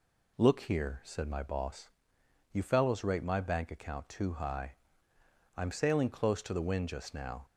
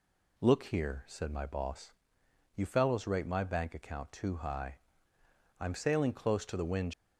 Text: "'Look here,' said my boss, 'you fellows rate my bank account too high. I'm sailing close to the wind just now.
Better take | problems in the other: first | stops before "just now"; at 6.9 s

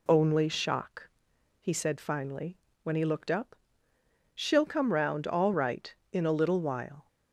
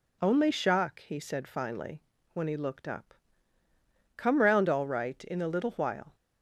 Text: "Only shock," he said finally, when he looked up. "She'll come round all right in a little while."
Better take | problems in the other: first | skips "She'll"; at 3.6 s

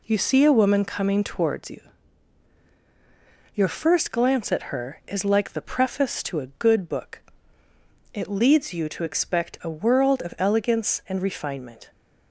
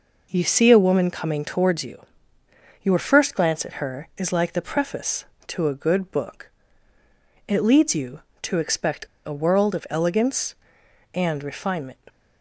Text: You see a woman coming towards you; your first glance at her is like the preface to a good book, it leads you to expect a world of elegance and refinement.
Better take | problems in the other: first | pauses between "expect" and "a"; slight; at 9.0 s; 0.19 s long

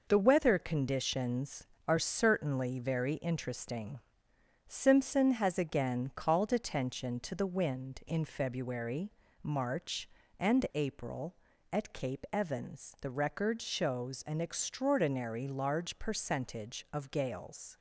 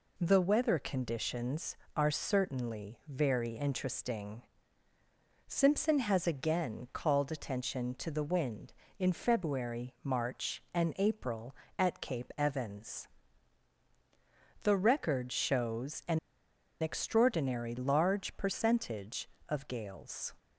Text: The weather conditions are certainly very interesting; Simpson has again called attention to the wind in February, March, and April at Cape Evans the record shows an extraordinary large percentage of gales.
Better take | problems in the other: first | pauses between "Evans" and "the"; strong; at 13.0 s; 1.5 s long // pauses between "an" and "extraordinary"; noticeable; at 16.1 s; 0.61 s long

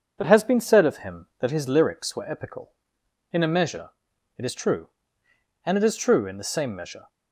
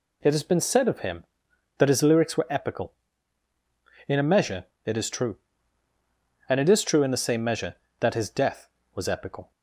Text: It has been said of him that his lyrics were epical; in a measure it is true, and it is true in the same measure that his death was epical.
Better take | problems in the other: second | pauses between "measure" and "it"; noticeable; at 3.8 s; 0.48 s long; slight in the second // stops before "that his death was epical"; at 7.0 s

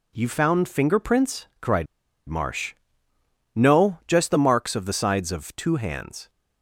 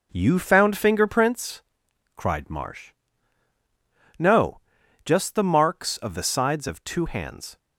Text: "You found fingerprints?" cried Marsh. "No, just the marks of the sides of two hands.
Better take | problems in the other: second | pauses between "cried" and "Marsh"; at 1.8 s; 0.43 s long

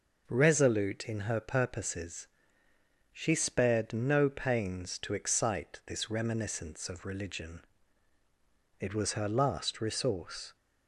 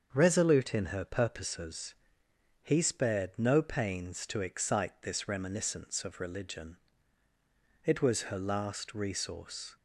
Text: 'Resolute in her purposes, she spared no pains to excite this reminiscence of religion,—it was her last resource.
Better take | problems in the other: first | starts louder than the rest; until 1.1 s; 7 dB // says "he" for "she"; at 2.6 s

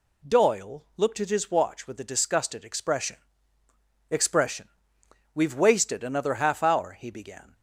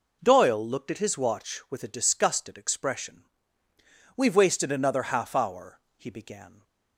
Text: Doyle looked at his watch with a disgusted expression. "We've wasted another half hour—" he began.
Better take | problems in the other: second | says "expression" twice; at 4.1 s

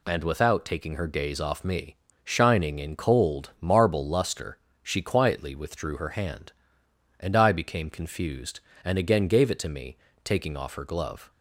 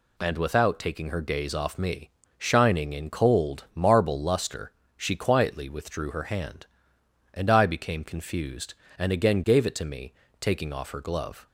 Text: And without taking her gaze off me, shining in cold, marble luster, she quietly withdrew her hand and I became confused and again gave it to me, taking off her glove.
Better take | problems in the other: neither | none

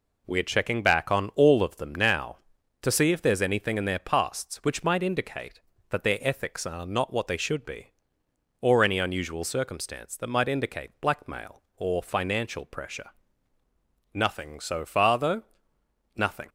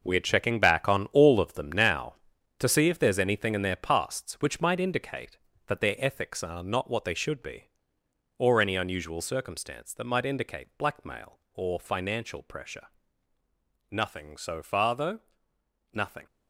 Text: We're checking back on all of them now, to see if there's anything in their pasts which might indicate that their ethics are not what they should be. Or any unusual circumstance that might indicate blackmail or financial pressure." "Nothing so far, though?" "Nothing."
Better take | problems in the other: first | gets quieter; strong; throughout; 11 dB

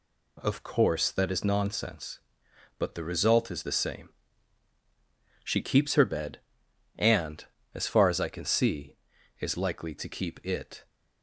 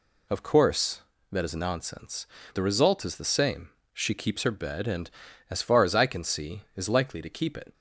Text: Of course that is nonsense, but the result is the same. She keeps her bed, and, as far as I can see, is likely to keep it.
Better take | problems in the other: first | skips "but"; at 2.4 s

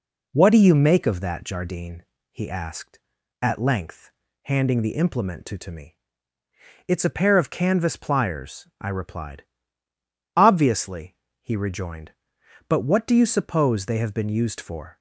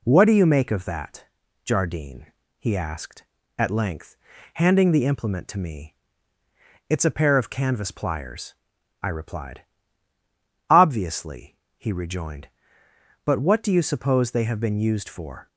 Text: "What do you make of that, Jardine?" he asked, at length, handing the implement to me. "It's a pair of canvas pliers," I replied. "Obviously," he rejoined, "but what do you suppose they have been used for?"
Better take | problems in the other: second | says "to" twice; at 5.5 s

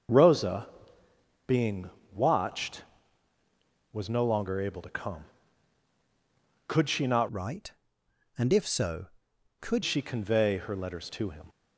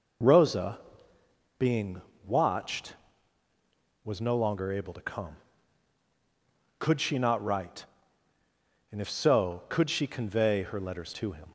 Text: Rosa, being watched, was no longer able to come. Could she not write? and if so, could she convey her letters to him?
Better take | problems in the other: second | pauses between "being" and "watched"; slight; at 1.8 s; 0.24 s long; slight in the second // changes voice from "write" to "could"; from 7.2 to 9.8 s; 2.6 s long

